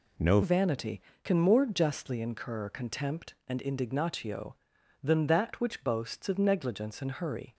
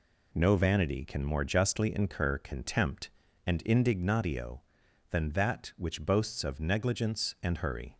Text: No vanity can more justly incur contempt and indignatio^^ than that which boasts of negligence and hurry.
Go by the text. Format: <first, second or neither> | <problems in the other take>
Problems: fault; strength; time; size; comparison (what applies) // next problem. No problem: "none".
second | changes voice at "vanity"; from 0.4 s on; 7.1 s long